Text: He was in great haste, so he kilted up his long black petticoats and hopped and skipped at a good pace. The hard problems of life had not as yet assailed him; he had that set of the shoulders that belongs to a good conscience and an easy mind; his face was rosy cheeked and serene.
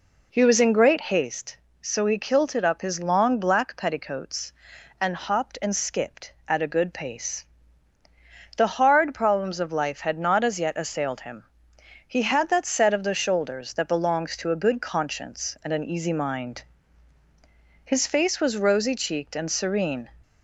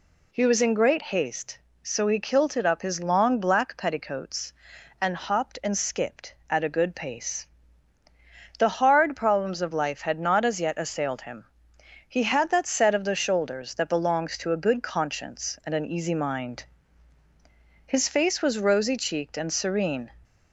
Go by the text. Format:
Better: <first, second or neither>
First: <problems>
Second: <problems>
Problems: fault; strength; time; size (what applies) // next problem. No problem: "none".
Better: second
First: starts louder than the rest; until 1.3 s; 4 dB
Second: none